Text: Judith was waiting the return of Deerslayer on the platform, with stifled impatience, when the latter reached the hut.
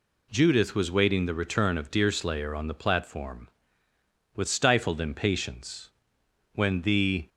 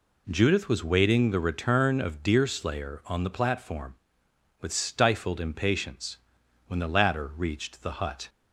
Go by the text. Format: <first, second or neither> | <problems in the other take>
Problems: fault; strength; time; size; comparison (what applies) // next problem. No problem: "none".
second | stops before "latter reached the hut"; at 7.2 s